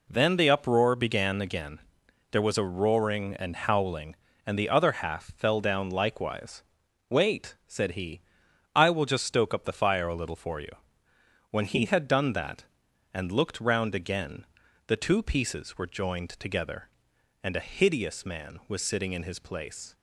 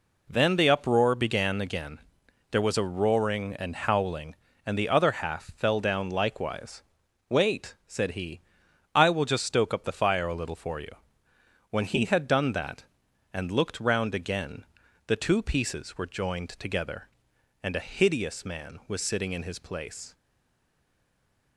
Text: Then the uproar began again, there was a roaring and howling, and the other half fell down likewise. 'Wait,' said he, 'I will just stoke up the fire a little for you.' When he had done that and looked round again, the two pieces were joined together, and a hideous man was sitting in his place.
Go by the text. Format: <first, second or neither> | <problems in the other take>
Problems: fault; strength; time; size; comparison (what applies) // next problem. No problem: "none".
first | stays silent after the last word; noticeable; from 20.1 s on; 1.4 s long